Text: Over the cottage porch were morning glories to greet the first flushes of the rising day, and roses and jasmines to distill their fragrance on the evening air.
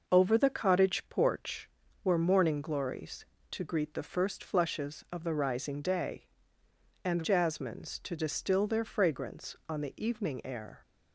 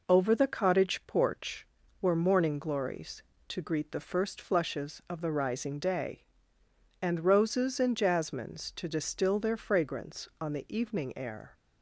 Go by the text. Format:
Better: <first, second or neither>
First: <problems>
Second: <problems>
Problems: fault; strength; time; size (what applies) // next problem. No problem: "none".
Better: second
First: skips "roses and"; at 7.2 s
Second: none